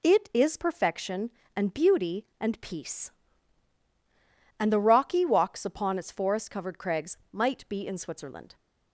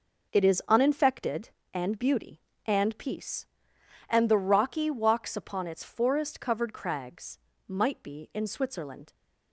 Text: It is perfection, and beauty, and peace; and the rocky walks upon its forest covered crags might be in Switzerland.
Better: first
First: pauses between "crags" and "might"; slight; at 7.1 s; 0.16 s long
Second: starts louder than the rest; noticeable; until 1.3 s; 6 dB // says "uninfected" for "perfection"; at 0.6 s // pauses between "crags" and "might"; slight; at 7.3 s; 0.28 s long

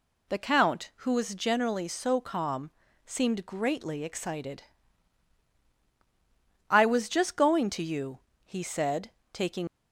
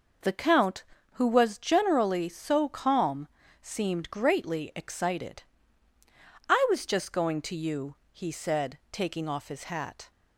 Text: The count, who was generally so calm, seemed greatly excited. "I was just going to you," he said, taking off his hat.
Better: second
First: stops before "off his hat"; at 9.6 s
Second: none

